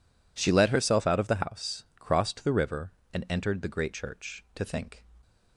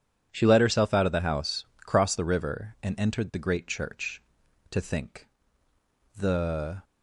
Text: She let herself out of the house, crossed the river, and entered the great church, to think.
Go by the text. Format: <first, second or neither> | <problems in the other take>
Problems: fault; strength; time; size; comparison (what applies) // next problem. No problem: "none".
first | goes on to say "The"; noticeable; from 6.1 s on; 0.68 s long